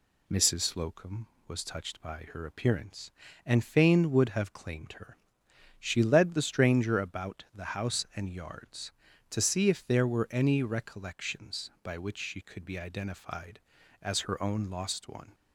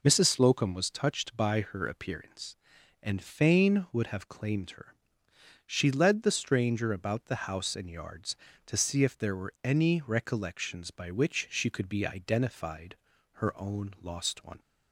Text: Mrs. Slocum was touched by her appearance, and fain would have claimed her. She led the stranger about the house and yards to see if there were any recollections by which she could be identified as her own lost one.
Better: first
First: none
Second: skips "as"; at 13.1 s

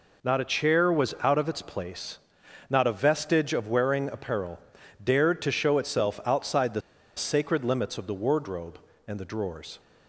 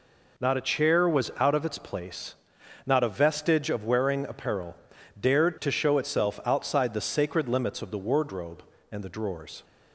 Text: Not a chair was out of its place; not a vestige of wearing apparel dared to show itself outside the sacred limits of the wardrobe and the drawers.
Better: second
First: pauses between "apparel" and "dared"; at 4.5 s; 0.44 s long // pauses between "the" and "sacred"; at 6.7 s; 0.36 s long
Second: pauses between "apparel" and "dared"; at 4.7 s; 0.44 s long

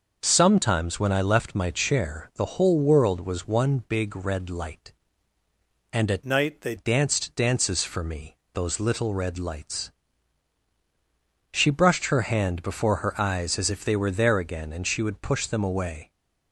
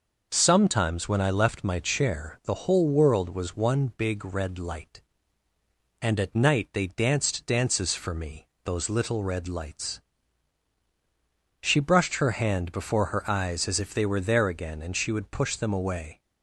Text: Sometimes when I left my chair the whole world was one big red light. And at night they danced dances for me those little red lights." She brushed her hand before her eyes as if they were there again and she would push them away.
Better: second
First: starts louder than the rest; noticeable; until 1.2 s; 6 dB // changes voice from "night" to "they"; from 6.2 to 6.7 s; 0.5 s long // pauses between "me" and "those"; slight; at 8.3 s; 0.18 s long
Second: pauses between "me" and "those"; slight; at 8.4 s; 0.18 s long

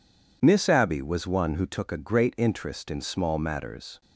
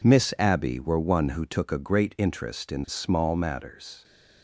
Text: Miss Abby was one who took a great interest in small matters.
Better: first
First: none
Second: says "were" for "was"; at 0.8 s

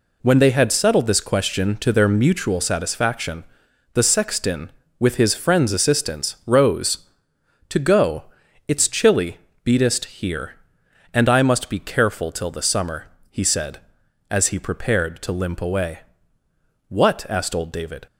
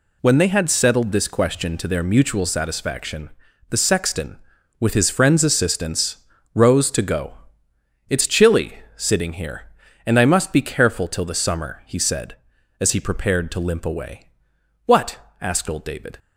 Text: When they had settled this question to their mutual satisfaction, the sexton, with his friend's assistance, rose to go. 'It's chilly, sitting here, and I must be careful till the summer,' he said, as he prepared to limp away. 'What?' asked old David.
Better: second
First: says "beatest" for "sitting"; at 9.6 s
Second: none

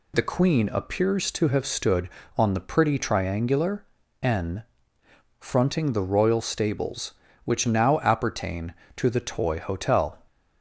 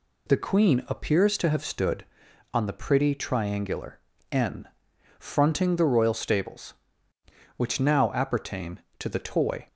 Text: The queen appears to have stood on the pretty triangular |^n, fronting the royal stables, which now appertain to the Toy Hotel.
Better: first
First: none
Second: stops before "Hotel"; at 9.6 s

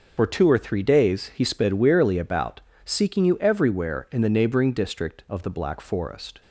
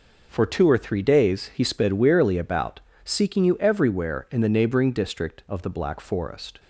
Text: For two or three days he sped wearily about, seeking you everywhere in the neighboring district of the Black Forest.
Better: second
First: loses the start of "For"; at 0.1 s; 70 ms // starts louder than the rest; until 1.1 s; 6.5 dB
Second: none

